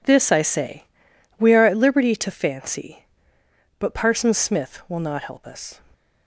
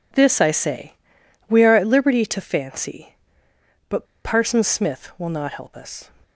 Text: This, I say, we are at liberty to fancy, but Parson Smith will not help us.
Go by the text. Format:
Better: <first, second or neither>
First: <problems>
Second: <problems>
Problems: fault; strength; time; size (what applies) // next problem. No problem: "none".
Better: first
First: none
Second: pauses between "but" and "Parson"; slight; at 4.0 s; 0.20 s long